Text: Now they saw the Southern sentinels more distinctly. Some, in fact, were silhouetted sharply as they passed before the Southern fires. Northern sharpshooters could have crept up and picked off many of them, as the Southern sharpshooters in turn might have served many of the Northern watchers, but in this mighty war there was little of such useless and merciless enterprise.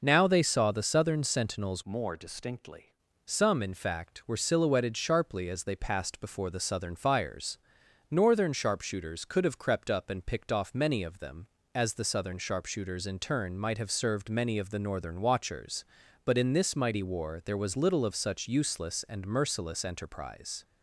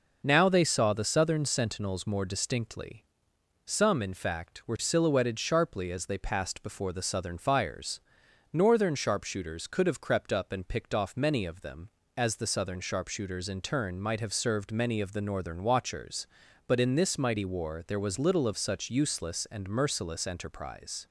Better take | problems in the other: second | changes voice from "more" to "distinctly"; from 1.8 to 2.9 s; 1.1 s long

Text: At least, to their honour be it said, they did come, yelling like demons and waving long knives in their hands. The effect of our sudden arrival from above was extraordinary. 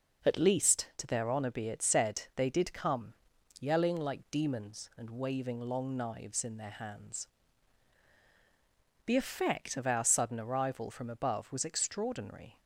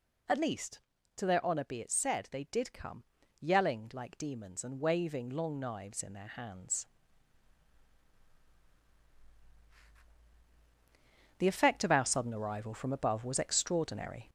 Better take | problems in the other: first | gets louder; slight; throughout; 3.5 dB

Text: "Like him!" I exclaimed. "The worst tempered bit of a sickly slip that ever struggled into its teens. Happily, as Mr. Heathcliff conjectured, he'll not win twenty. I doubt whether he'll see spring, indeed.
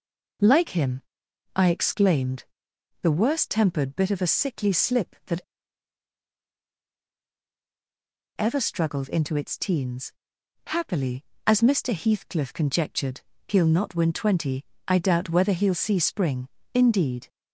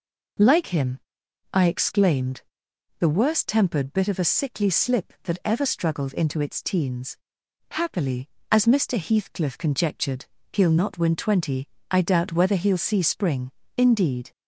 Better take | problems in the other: second | pauses between "that" and "ever"; strong; at 5.4 s; 2.9 s long

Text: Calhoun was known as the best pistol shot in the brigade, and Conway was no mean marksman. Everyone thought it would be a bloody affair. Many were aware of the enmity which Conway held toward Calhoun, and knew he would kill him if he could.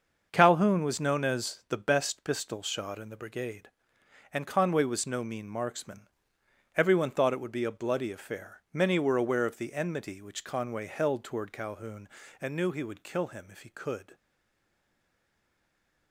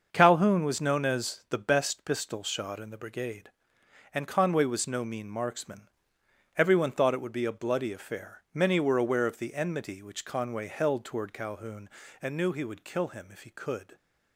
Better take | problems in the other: second | starts louder than the rest; until 1.3 s; 6.5 dB; also in the second // stays silent after the last word; noticeable; from 14.1 s on; 2.0 s long

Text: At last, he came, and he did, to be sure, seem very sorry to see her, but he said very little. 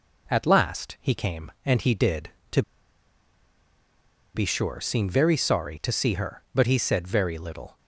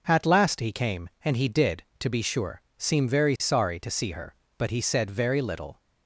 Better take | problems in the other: second | pauses between "to" and "be"; strong; at 2.6 s; 1.7 s long

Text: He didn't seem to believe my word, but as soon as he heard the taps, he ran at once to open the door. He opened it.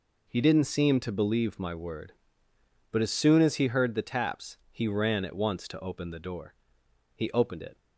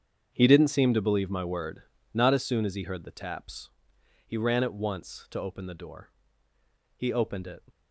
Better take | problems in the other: first | starts louder than the rest; strong; until 1.3 s; 7.5 dB // says "not" for "but"; at 2.1 s

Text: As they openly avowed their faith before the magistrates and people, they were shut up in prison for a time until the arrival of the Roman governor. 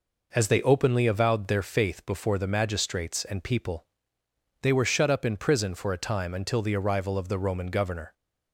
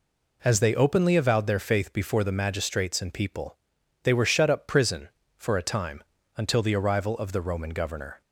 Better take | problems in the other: first | skips "in"; at 4.6 s // pauses between "time" and "until"; slight; at 6.0 s; 0.32 s long

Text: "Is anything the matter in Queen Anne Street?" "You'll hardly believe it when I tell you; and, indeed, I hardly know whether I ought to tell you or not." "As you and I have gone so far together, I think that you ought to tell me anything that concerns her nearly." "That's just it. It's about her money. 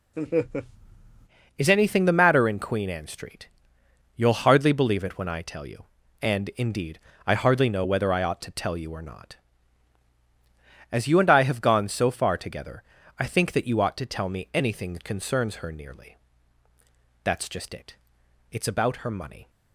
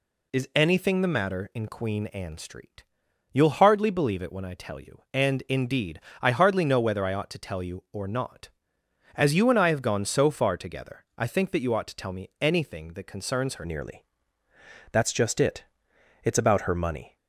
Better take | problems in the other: first | changes voice at "nearly"; from 13.6 s on; 3.5 s long

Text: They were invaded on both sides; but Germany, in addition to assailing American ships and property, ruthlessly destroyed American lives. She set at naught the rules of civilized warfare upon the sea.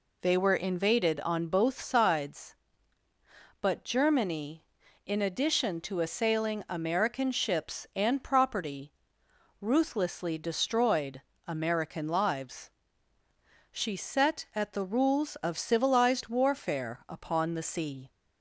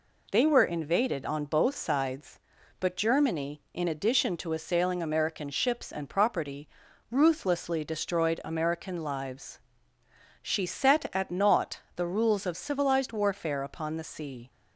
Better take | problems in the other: second | pauses between "destroyed" and "American"; slight; at 11.2 s; 0.24 s long // skips "naught"; at 14.7 s

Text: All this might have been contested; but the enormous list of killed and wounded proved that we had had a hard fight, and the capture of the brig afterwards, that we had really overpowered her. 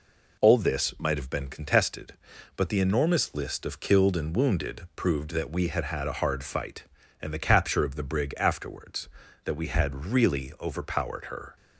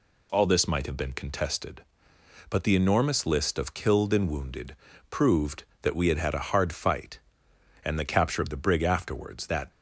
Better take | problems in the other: first | pauses between "wounded" and "proved"; slight; at 4.7 s; 0.34 s long // stops before "we had really overpowered her"; at 9.7 s

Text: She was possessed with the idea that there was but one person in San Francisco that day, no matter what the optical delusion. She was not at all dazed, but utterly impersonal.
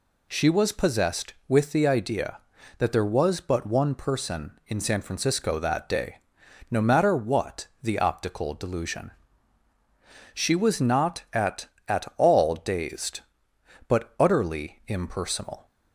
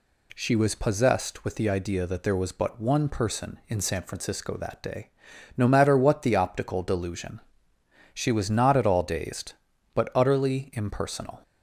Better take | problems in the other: second | pauses between "what" and "the"; slight; at 7.6 s; 0.16 s long // says "at" twice; at 11.8 s

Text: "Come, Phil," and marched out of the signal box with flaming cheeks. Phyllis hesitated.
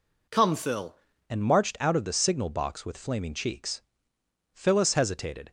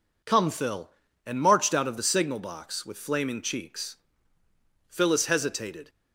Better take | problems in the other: second | changes voice at "and"; from 1.2 s on; 4.3 s long

